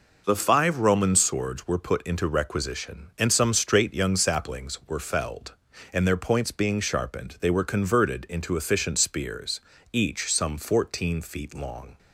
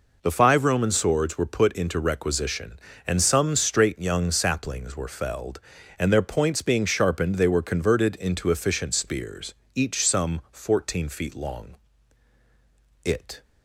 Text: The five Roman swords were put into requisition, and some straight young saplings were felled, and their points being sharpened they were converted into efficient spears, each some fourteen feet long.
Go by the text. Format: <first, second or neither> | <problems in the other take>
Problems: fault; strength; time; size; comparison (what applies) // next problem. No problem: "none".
first | goes on to say "It"; slight; from 13.0 s on; 0.38 s long